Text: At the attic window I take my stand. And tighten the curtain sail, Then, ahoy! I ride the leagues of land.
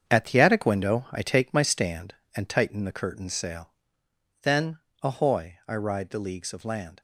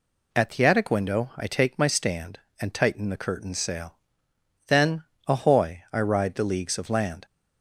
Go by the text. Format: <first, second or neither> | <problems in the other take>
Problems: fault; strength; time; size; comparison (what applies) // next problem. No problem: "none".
second | gets quieter; strong; throughout; 8 dB